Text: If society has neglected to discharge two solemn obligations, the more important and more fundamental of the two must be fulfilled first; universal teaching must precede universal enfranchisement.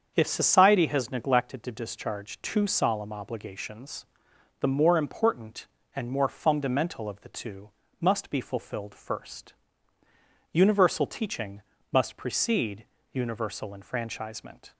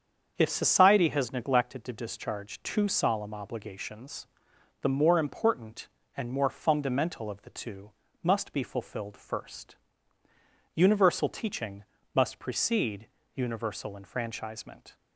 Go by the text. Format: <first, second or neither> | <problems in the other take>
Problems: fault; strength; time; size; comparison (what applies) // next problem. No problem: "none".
neither | starts louder than the rest; strong; the same in both // pauses between "two" and "must"; slight; the same in both // pauses between "teaching" and "must"; slight; the same in both // pauses between "precede" and "universal"; slight; the same in both